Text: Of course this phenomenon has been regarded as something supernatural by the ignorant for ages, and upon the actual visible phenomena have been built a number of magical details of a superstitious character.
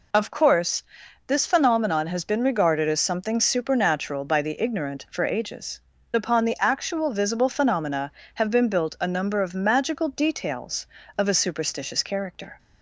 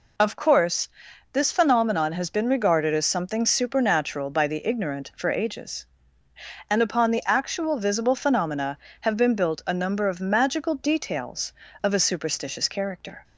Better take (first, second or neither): second